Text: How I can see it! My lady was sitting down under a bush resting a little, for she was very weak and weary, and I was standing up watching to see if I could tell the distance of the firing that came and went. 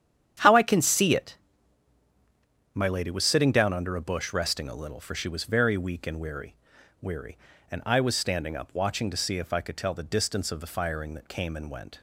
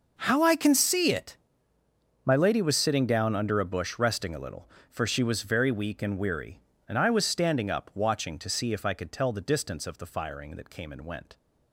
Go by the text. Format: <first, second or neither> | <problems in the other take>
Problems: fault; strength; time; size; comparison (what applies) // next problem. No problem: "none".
second | starts louder than the rest; strong; until 2.7 s; 9.5 dB // says "weary" twice; at 7.0 s